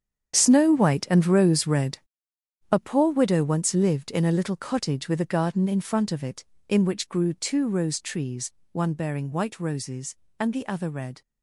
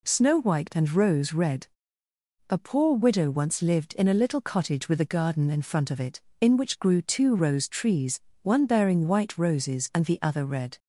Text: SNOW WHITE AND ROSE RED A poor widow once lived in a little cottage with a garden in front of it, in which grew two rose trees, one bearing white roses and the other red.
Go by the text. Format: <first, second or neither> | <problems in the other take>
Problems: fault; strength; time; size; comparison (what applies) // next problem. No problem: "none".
second | gets quieter; strong; throughout; 12.5 dB // pauses between "RED" and "A"; noticeable; at 1.9 s; 0.73 s long; noticeable in the second